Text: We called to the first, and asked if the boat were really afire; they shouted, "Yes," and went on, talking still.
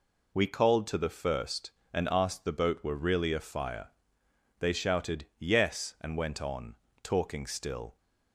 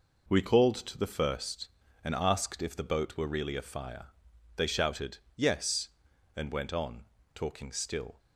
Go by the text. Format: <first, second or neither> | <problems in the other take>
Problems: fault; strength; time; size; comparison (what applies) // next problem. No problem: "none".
second | skips "if"; at 2.4 s